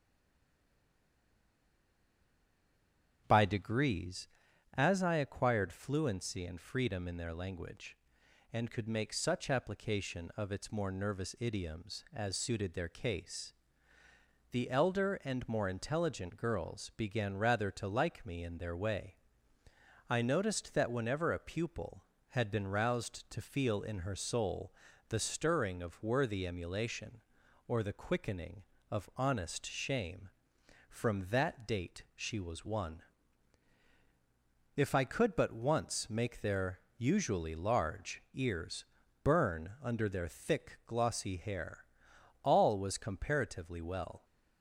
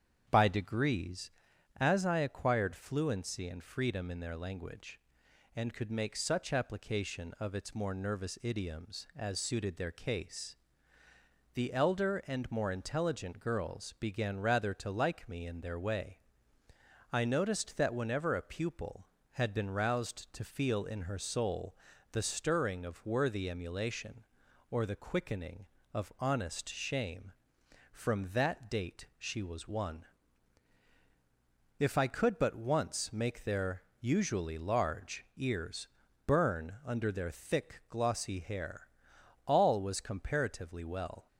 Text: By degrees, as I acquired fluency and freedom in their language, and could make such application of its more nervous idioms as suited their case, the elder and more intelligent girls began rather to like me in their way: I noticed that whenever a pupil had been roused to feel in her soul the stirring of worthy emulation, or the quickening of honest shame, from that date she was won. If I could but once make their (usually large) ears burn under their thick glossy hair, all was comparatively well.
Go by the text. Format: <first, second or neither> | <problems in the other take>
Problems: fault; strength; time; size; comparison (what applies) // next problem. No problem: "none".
second | stays silent before the first word; strong; until 3.2 s; 3.2 s long // starts louder than the rest; strong; until 4.2 s; 8 dB; strong in the second // pauses between "soul" and "the"; slight; at 24.7 s; 0.34 s long; slight in the second // pauses between "ears" and "burn"; at 38.8 s; 0.38 s long; also in the second